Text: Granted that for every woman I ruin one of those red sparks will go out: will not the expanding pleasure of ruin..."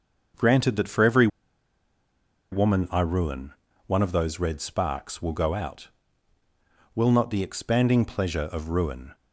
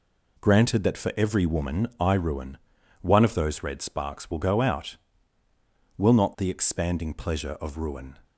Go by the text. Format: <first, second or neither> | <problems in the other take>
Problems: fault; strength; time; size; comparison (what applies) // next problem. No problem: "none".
second | starts louder than the rest; until 2.6 s; 6.5 dB // pauses between "every" and "woman"; strong; at 1.2 s; 1.2 s long // pauses between "ruin" and "one"; slight; at 3.5 s; 0.34 s long; also in the second